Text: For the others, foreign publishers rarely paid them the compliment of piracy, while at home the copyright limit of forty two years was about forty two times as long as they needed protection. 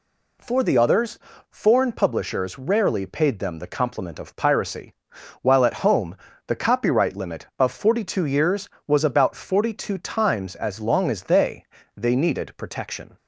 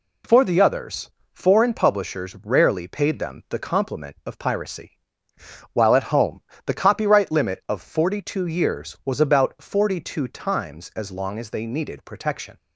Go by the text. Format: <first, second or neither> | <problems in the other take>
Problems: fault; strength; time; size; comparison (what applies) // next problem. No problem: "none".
second | pauses between "home" and "the"; slight; at 6.1 s; 0.32 s long; slight in the second // says "they" twice; at 11.9 s